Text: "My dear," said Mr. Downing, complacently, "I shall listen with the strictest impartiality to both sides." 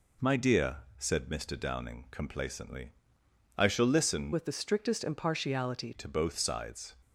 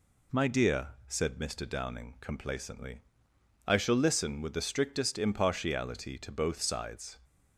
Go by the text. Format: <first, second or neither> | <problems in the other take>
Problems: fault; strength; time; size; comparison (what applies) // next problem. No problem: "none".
second | changes voice from "with" to "impartiality"; from 4.3 to 5.9 s; 1.6 s long